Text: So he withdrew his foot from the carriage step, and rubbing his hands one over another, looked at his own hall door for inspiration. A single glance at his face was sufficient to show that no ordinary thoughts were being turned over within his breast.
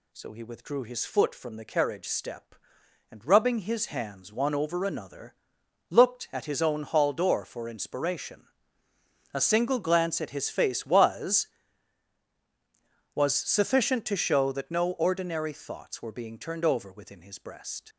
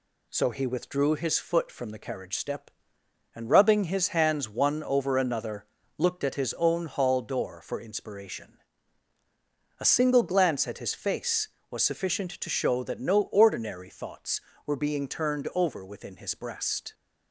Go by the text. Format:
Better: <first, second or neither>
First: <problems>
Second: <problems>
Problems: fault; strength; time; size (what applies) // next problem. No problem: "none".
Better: second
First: says "was" twice; at 13.1 s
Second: none